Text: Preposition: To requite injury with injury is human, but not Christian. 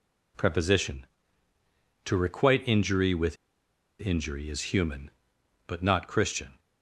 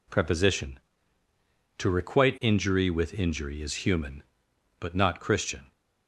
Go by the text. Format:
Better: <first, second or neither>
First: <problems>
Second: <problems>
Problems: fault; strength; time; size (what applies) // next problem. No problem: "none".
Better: second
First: pauses between "with" and "injury"; noticeable; at 3.3 s; 0.64 s long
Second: none